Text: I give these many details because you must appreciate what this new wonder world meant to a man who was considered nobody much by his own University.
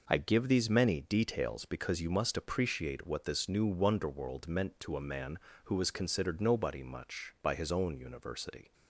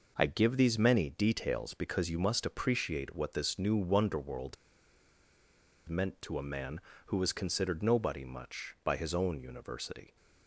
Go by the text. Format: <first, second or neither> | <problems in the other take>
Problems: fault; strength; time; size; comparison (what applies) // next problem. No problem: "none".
first | pauses between "world" and "meant"; strong; at 4.5 s; 1.3 s long